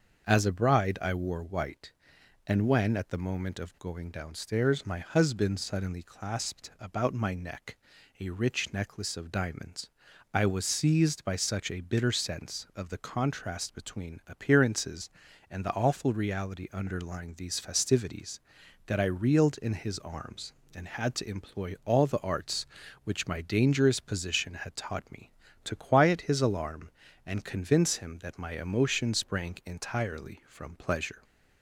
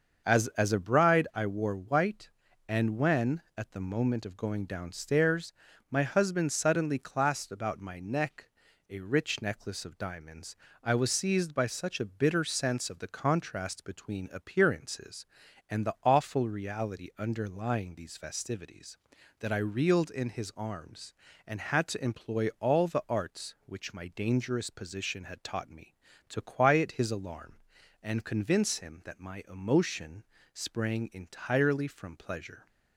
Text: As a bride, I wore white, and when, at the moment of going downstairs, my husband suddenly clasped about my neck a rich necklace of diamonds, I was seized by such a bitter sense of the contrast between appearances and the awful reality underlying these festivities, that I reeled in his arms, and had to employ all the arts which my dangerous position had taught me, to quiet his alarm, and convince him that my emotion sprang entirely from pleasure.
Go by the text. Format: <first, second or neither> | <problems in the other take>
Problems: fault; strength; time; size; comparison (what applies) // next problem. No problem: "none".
first | starts louder than the rest; until 1.2 s; 6.5 dB; also in the first // says "As" twice; at 0.4 s // pauses between "neck" and "a"; at 8.4 s; 0.40 s long; also in the first // pauses between "emotion" and "sprang"; slight; at 30.2 s; 0.28 s long